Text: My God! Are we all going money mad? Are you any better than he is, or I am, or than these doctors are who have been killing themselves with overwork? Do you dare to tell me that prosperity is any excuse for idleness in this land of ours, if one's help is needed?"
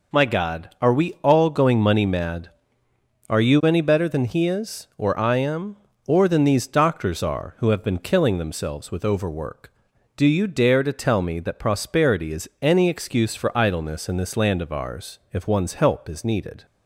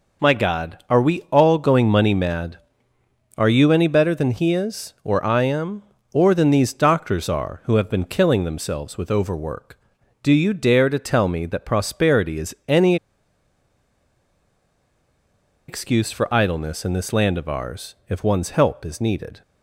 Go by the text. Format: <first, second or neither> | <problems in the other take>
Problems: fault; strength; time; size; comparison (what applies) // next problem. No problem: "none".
first | pauses between "any" and "excuse"; strong; at 12.9 s; 2.7 s long